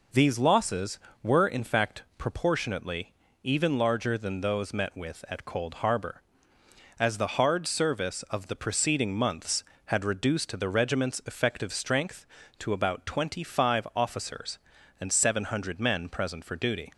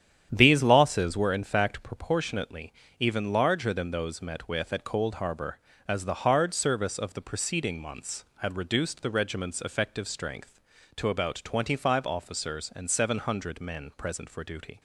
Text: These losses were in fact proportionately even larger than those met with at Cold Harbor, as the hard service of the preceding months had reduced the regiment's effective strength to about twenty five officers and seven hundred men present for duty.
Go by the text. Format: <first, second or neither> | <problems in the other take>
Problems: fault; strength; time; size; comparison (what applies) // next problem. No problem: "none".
first | starts louder than the rest; strong; until 1.3 s; 9.5 dB // pauses between "proportionately" and "even"; slight; at 2.7 s; 0.28 s long; slight in the first